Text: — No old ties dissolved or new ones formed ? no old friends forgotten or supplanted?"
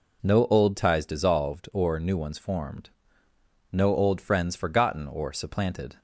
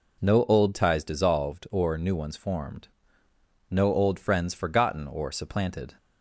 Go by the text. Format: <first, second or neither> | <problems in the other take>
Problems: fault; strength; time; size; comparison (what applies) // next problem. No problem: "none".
neither | none